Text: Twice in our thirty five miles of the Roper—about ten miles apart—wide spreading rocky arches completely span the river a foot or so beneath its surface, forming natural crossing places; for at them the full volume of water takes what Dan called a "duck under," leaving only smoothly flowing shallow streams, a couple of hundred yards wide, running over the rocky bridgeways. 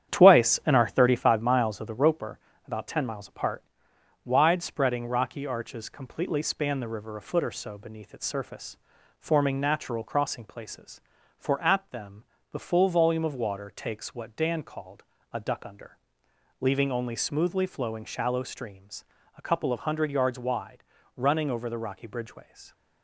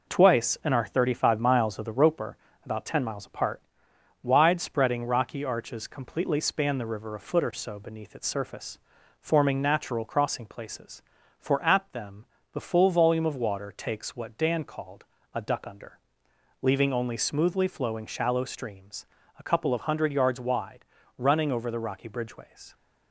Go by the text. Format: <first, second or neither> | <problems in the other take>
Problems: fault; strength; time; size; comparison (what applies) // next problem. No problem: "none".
second | starts louder than the rest; strong; until 1.4 s; 9.5 dB // pauses between "them" and "the"; slight; at 12.2 s; 0.28 s long; slight in the second // pauses between "called" and "a"; slight; at 15.0 s; 0.32 s long; slight in the second